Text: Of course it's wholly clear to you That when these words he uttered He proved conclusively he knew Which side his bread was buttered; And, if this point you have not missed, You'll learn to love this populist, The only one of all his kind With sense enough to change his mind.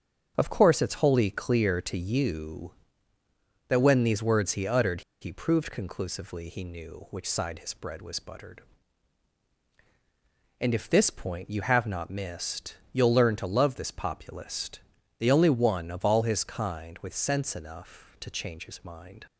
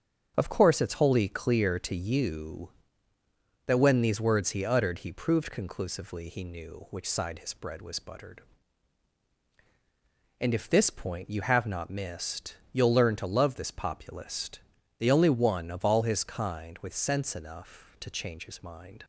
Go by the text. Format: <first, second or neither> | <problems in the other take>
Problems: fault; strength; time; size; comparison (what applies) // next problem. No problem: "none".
second | starts louder than the rest; strong; until 1.3 s; 8 dB; strong in the second // pauses between "uttered" and "He"; slight; at 5.0 s; 0.20 s long